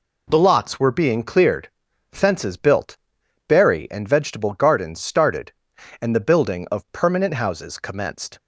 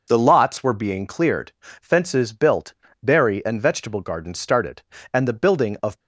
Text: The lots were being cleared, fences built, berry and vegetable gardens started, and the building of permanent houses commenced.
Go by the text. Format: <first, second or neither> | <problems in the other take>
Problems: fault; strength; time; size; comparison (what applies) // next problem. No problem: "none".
first | stops before "permanent houses commenced"; at 6.0 s